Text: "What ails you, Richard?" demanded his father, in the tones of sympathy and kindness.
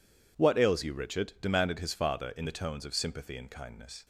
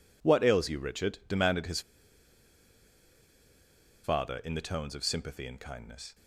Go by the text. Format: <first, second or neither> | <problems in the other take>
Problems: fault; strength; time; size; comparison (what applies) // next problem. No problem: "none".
first | pauses between "his" and "father"; strong; at 1.8 s; 2.2 s long